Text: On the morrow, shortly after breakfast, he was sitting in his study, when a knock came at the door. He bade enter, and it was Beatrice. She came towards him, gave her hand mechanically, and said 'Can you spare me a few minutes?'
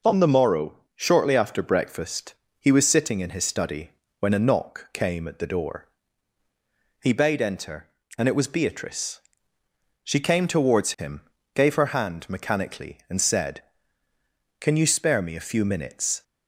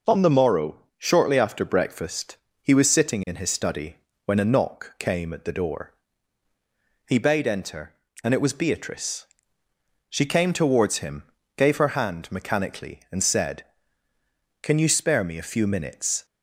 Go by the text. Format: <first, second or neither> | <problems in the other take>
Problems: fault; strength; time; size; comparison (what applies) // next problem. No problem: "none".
neither | none